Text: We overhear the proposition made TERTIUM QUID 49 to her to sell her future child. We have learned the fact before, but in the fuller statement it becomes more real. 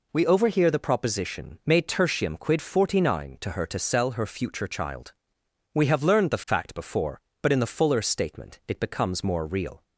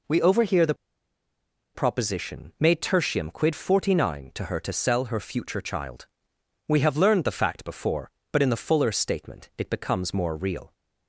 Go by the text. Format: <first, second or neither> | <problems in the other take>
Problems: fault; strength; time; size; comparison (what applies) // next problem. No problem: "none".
first | pauses between "the" and "proposition"; at 0.7 s; 1.0 s long